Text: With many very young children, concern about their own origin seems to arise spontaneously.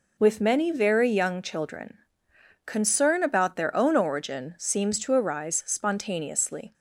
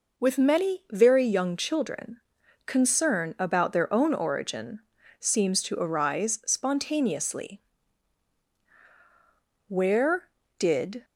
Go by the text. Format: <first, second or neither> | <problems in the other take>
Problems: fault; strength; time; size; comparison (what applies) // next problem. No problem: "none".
first | pauses between "origin" and "seems"; at 4.8 s; 0.40 s long // goes on to say "Where did"; from 9.6 s on; 1.3 s long